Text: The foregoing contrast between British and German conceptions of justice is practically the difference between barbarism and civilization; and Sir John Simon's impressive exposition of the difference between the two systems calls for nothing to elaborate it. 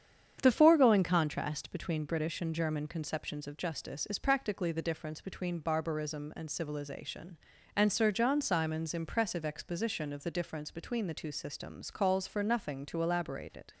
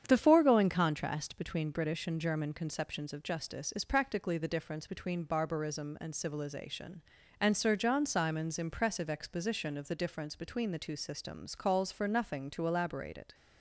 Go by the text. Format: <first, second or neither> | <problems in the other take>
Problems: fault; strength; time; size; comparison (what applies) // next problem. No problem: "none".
neither | starts louder than the rest; strong; the same in both